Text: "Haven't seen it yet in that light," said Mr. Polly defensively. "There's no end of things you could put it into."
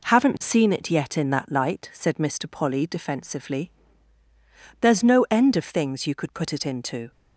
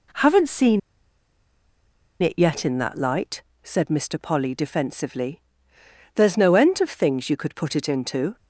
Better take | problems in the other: first | pauses between "seen" and "it"; strong; at 0.7 s; 1.4 s long

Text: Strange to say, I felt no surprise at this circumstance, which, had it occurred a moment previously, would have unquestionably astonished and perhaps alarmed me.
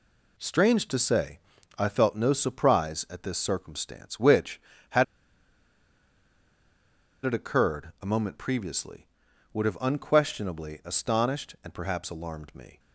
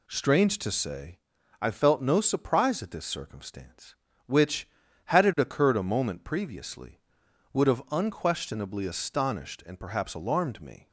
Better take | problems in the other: second | pauses between "had" and "it"; strong; at 5.0 s; 2.2 s long

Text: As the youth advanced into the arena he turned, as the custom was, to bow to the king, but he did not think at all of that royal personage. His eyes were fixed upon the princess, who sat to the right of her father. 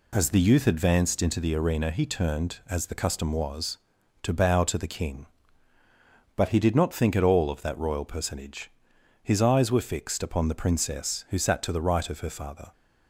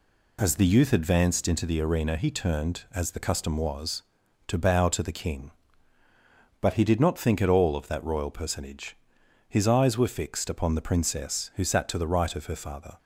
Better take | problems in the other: neither | none

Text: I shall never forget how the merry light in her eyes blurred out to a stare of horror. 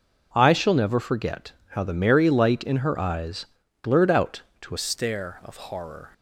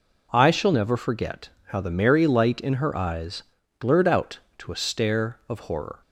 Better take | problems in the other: second | pauses between "forget" and "how"; slight; at 1.5 s; 0.18 s long; slight in the second // pauses between "eyes" and "blurred"; slight; at 3.4 s; 0.36 s long; slight in the second // changes voice at "stare"; from 4.7 s on; 1.4 s long

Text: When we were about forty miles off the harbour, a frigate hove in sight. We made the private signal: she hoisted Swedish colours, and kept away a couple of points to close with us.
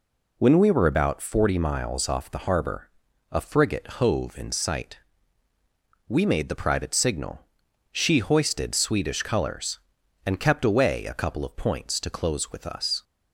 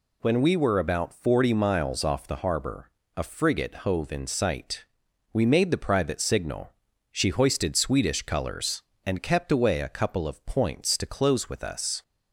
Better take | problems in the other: neither | none

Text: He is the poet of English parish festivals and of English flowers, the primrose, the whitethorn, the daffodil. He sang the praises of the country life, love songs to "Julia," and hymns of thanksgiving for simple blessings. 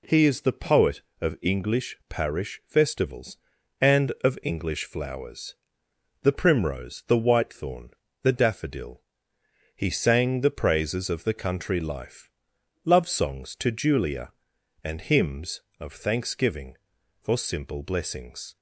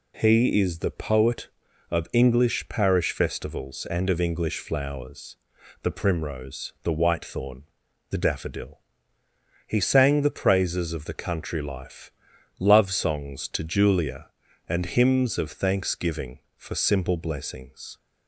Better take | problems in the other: neither | none

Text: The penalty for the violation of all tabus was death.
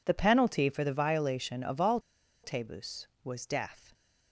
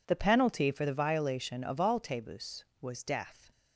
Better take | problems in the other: second | pauses between "all" and "tabus"; at 1.9 s; 0.44 s long

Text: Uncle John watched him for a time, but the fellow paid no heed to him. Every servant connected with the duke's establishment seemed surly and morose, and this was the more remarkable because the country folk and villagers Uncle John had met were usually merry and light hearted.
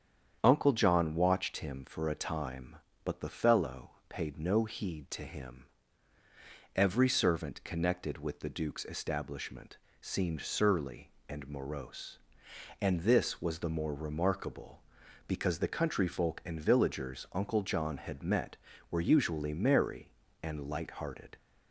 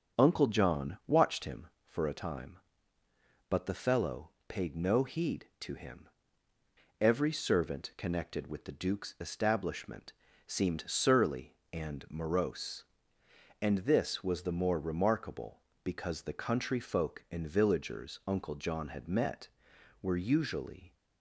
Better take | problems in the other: first | starts louder than the rest; strong; until 1.2 s; 7 dB; strong in the first // pauses between "fellow" and "paid"; slight; at 4.2 s; 0.18 s long; slight in the first // pauses between "establishment" and "seemed"; slight; at 10.1 s; 0.34 s long; slight in the first // stops before "merry and light hearted"; at 20.9 s

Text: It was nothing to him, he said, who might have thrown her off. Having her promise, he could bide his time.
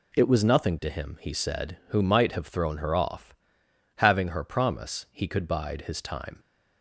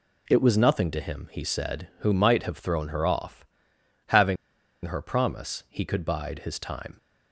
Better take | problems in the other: first | pauses between "Having" and "her"; noticeable; at 4.3 s; 0.49 s long

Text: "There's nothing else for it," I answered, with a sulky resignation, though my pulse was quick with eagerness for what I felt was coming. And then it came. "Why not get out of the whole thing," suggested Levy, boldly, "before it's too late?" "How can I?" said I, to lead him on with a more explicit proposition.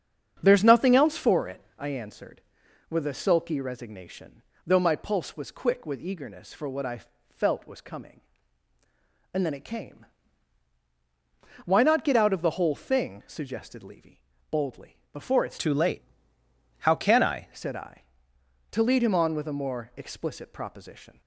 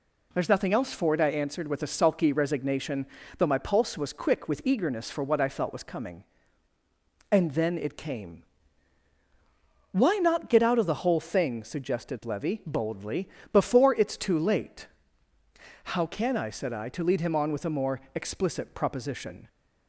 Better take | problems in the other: second | starts louder than the rest; strong; until 1.4 s; 7 dB // pauses between "I" and "felt"; slight; at 7.0 s; 0.28 s long // changes voice from "too" to "I"; from 15.5 to 17.4 s; 1.9 s long

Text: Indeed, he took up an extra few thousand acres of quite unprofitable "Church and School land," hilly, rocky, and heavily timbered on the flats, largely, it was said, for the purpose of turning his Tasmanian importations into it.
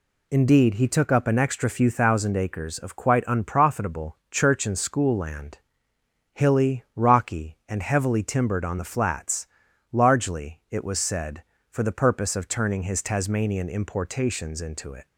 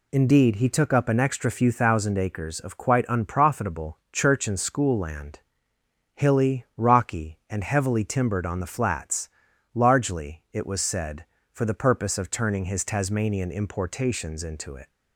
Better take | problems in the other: neither | none

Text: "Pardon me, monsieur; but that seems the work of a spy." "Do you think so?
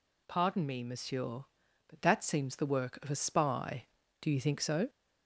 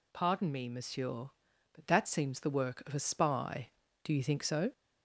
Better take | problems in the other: neither | none

